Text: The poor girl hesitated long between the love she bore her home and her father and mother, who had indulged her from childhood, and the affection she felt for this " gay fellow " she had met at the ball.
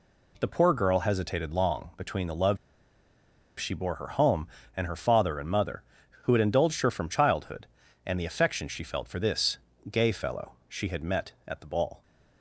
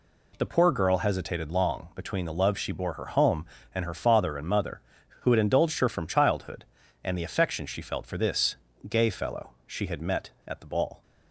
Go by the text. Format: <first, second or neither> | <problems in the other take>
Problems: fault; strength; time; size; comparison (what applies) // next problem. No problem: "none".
second | pauses between "love" and "she"; at 2.5 s; 1.0 s long